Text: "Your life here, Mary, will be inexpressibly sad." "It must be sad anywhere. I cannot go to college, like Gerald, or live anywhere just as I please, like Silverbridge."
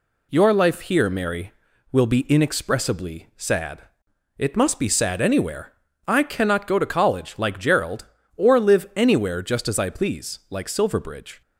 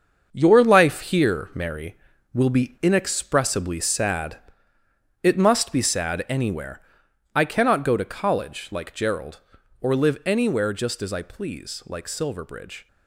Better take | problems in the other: first | gets quieter; strong; throughout; 8.5 dB

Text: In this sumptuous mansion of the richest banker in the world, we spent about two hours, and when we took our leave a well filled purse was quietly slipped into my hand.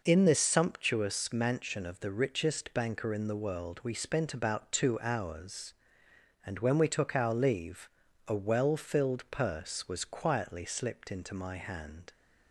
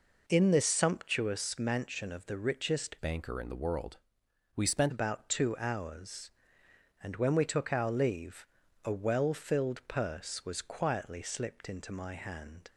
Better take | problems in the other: first | changes voice from "banker" to "spent"; from 2.9 to 4.9 s; 2.0 s long // pauses between "leave" and "a"; at 8.4 s; 0.40 s long; also in the first

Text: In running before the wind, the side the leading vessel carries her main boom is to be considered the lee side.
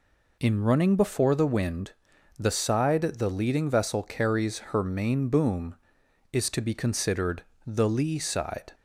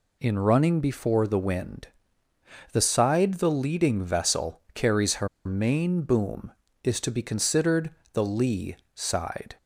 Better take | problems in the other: first | pauses between "her" and "main"; slight; at 5.2 s; 0.17 s long // pauses between "considered" and "the"; slight; at 7.9 s; 0.22 s long; slight in the first // pauses between "lee" and "side"; slight; at 8.7 s; 0.20 s long

